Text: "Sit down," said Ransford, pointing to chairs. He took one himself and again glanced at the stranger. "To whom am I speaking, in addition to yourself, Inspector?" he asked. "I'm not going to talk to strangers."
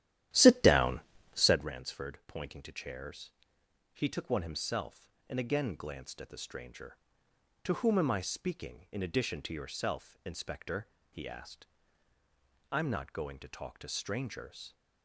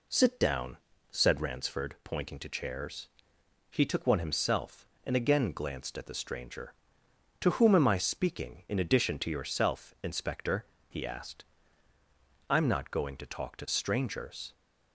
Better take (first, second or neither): second